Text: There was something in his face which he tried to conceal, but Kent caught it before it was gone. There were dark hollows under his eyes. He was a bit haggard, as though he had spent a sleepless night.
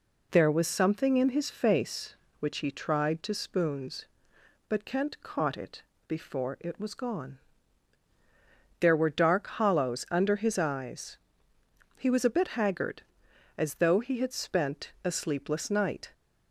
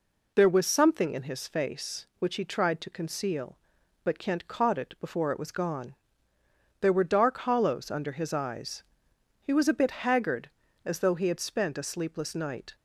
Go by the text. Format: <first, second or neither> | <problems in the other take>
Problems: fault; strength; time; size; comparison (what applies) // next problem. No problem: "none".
second | says "spoons" for "conceal"; at 3.3 s // pauses between "it" and "before"; slight; at 5.8 s; 0.24 s long